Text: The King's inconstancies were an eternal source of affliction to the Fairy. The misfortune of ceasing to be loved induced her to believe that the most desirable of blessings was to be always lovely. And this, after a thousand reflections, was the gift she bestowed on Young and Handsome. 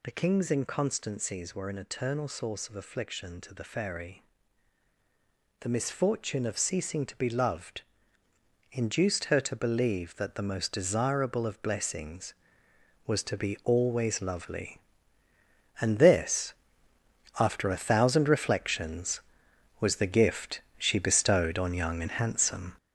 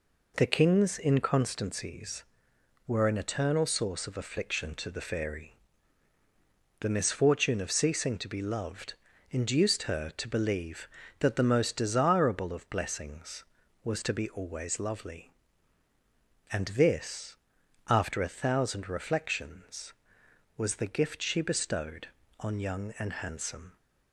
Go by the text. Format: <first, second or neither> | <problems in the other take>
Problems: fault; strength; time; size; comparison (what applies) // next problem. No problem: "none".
second | gets louder; throughout; 7 dB // pauses between "loved" and "induced"; noticeable; at 7.8 s; 0.90 s long; slight in the second // pauses between "gift" and "she"; slight; at 20.6 s; 0.16 s long